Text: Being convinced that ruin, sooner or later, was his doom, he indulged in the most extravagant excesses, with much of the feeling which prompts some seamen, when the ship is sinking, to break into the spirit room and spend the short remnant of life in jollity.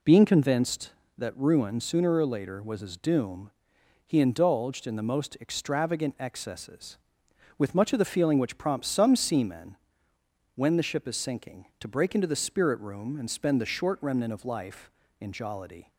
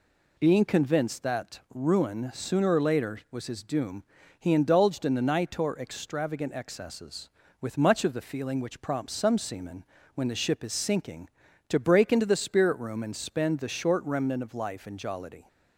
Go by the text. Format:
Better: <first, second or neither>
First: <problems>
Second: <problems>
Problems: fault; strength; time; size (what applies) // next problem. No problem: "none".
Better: first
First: none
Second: says "nitor" for "most"; at 5.2 s